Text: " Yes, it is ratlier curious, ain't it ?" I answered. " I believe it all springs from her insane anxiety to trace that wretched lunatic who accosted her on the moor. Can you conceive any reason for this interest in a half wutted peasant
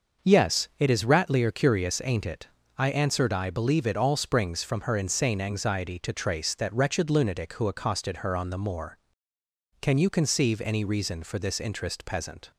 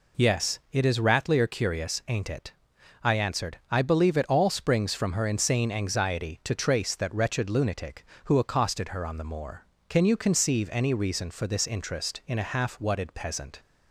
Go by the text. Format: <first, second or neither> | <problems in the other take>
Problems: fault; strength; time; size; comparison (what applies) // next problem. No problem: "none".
second | starts louder than the rest; noticeable; until 1.3 s; 6 dB // skips "in a half wutted"; at 12.0 s